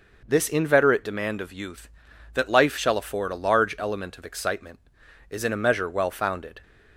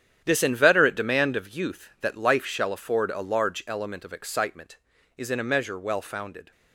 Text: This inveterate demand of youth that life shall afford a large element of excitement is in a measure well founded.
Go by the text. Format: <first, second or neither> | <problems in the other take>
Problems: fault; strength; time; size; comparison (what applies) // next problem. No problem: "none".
first | gets quieter; strong; throughout; 11.5 dB